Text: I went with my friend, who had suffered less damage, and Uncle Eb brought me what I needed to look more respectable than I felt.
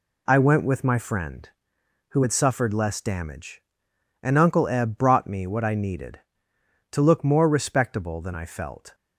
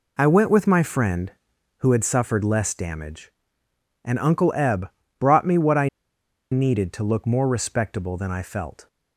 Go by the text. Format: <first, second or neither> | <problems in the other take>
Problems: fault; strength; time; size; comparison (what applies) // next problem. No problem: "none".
first | pauses between "Eb" and "brought"; slight; at 4.8 s; 0.30 s long // pauses between "I" and "needed"; noticeable; at 5.8 s; 0.64 s long